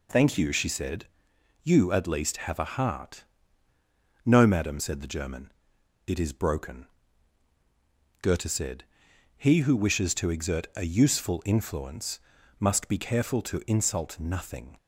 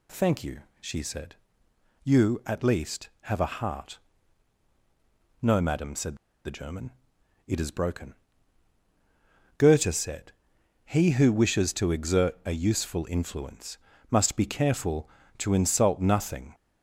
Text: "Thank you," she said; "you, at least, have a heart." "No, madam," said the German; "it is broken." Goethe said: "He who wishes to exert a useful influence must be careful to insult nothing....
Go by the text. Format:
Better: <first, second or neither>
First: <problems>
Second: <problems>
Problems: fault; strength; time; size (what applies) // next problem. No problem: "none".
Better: first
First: pauses between "influence" and "must"; at 12.2 s; 0.38 s long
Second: pauses between "said" and "the"; slight; at 6.1 s; 0.28 s long // pauses between "influence" and "must"; slight; at 13.7 s; 0.32 s long